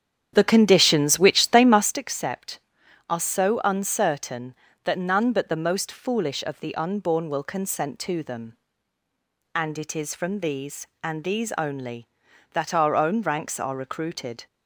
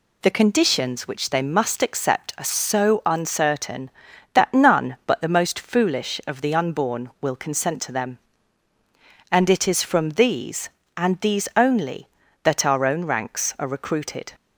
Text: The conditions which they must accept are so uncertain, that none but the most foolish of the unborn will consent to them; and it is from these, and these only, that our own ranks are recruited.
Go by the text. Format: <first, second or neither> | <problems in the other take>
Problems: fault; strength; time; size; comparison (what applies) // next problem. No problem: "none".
second | starts louder than the rest; strong; until 2.0 s; 9 dB